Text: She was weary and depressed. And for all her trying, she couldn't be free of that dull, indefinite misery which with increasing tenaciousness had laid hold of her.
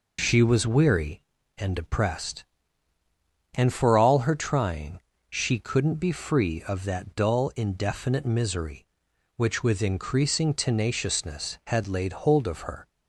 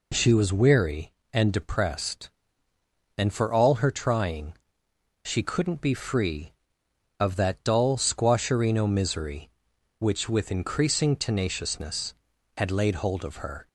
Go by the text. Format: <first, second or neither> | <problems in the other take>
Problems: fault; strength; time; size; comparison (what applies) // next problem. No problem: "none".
first | says "squasherino" for "indefinite"; at 7.9 s